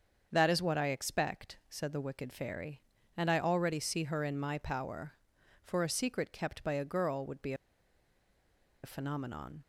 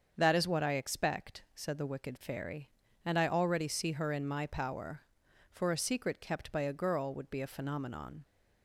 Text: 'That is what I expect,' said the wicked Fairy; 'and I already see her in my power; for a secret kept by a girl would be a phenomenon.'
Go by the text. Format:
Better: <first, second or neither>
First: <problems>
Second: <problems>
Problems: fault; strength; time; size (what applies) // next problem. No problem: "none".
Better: second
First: starts louder than the rest; until 1.3 s; 7 dB // pauses between "be" and "a"; strong; at 7.5 s; 1.2 s long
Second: starts louder than the rest; until 1.1 s; 7 dB